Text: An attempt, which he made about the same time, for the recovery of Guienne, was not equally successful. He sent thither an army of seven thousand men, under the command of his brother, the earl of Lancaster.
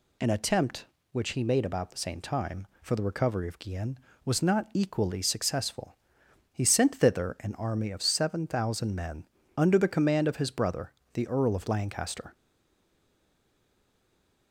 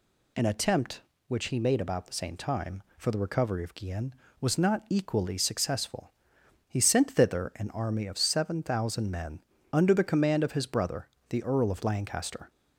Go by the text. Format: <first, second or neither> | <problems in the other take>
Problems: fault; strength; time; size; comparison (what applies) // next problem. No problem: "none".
second | stays silent after the last word; from 12.3 s on; 2.2 s long